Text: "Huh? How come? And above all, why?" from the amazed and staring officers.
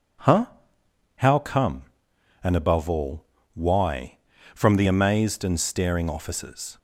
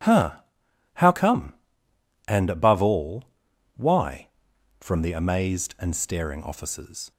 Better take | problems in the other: neither | none

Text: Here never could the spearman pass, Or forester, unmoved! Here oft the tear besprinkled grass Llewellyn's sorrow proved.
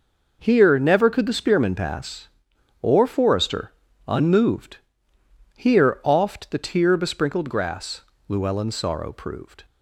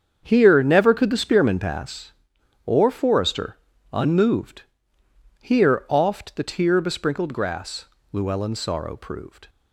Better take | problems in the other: first | starts louder than the rest; strong; until 1.8 s; 7.5 dB // pauses between "grass" and "Llewellyn's"; slight; at 7.8 s; 0.26 s long; slight in the first

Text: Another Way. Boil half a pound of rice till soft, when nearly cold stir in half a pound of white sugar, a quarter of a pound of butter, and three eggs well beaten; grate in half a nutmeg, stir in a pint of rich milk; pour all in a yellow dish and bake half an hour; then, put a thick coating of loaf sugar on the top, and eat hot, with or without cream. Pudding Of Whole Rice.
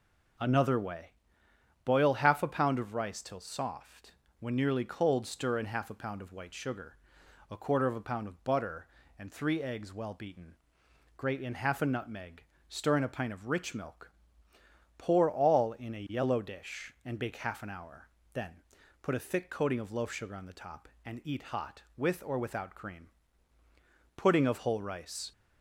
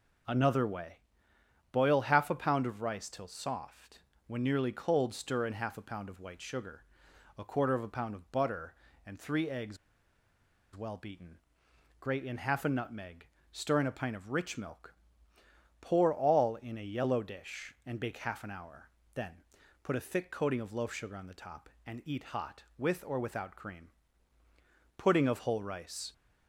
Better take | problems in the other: first | pauses between "eggs" and "well"; noticeable; at 9.7 s; 0.97 s long

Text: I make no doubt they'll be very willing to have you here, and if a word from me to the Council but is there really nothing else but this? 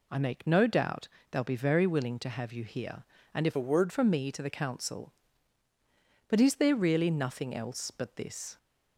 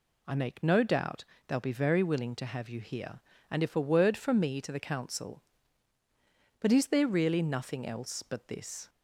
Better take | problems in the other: second | pauses between "doubt" and "they'll"; slight; at 1.0 s; 0.22 s long; slight in the second // changes voice from "a" to "word"; from 3.5 to 3.9 s; 0.4 s long

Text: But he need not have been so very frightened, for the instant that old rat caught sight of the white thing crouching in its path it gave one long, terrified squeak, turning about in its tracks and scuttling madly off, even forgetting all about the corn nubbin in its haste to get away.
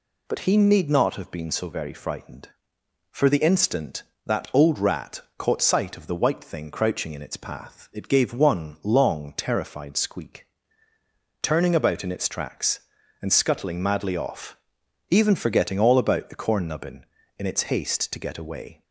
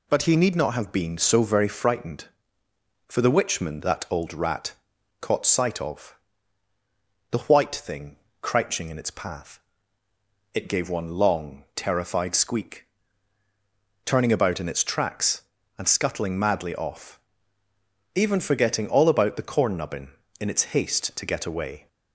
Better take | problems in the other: first | says "witchman" for "instant"; at 3.3 s // pauses between "rat" and "caught"; noticeable; at 4.7 s; 0.48 s long; slight in the first // pauses between "of" and "the"; at 6.1 s; 1.1 s long // pauses between "thing" and "crouching"; slight; at 8.1 s; 0.24 s long // pauses between "path" and "it"; noticeable; at 9.5 s; 0.94 s long

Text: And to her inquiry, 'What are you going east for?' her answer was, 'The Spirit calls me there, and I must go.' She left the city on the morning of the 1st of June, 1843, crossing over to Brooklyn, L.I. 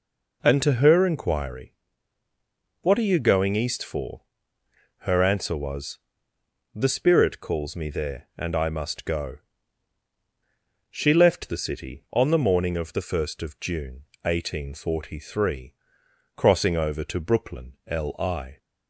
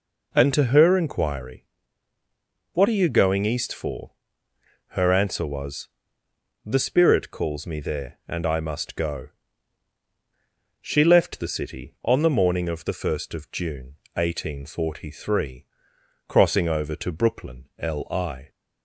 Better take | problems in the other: neither | none

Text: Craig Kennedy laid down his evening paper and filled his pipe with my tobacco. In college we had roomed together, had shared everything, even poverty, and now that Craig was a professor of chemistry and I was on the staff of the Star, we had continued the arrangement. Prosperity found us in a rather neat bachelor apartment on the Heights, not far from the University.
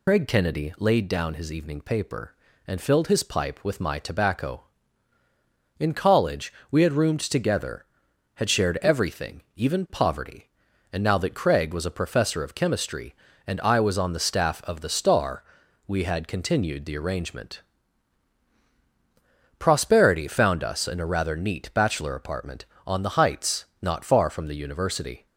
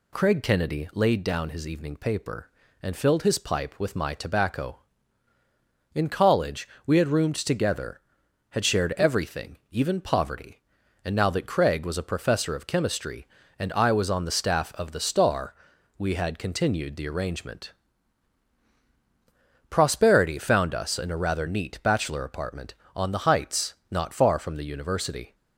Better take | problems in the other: second | loses the start of "Craig"; at 0.0 s; 100 ms // pauses between "college" and "we"; slight; at 6.5 s; 0.18 s long; slight in the second

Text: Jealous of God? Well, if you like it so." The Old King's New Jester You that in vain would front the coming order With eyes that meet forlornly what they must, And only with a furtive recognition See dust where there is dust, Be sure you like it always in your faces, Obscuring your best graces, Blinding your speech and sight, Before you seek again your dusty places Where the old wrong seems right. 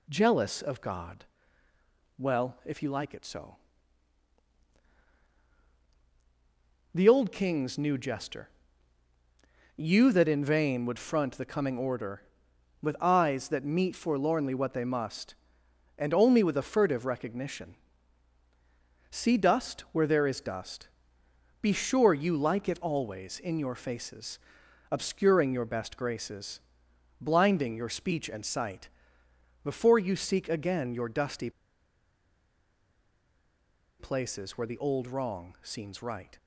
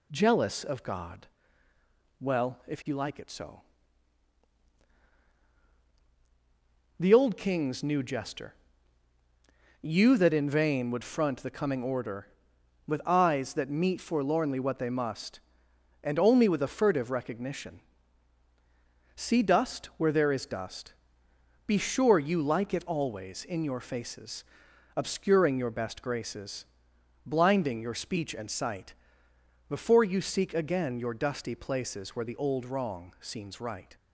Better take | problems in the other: second | pauses between "Jester" and "You"; strong; at 8.4 s; 1.2 s long; strong in the second // pauses between "recognition" and "See"; strong; at 17.7 s; 1.3 s long; strong in the second // pauses between "dusty" and "places"; strong; at 31.5 s; 2.4 s long

